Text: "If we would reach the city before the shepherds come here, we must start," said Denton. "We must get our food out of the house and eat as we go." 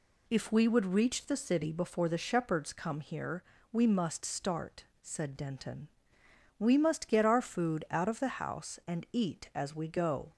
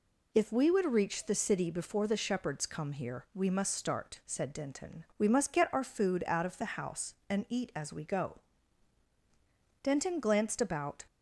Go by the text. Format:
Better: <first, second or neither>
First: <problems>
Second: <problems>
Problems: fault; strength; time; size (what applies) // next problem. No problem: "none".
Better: first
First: none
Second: goes on to say "Denton glanced about"; noticeable; from 9.8 s on; 1.2 s long